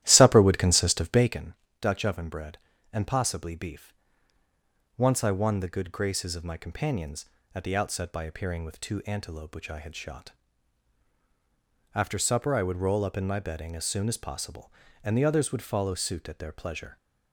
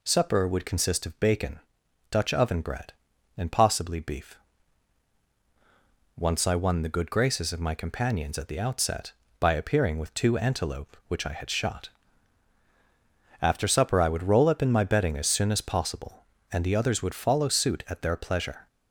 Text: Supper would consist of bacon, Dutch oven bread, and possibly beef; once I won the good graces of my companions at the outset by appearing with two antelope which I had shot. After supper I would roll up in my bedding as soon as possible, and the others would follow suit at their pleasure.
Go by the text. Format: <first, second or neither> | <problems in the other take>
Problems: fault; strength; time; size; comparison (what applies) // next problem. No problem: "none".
second | starts louder than the rest; strong; until 1.4 s; 13.5 dB